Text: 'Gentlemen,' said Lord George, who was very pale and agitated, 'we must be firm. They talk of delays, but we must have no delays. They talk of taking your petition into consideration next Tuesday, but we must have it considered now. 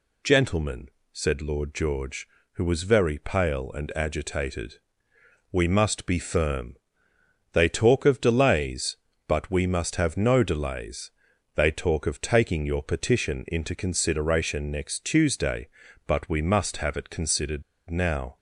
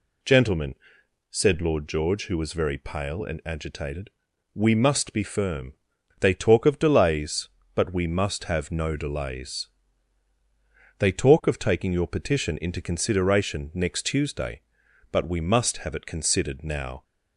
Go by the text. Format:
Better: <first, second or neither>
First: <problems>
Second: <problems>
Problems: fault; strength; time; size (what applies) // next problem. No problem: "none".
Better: second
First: pauses between "considered" and "now"; slight; at 17.6 s; 0.26 s long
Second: none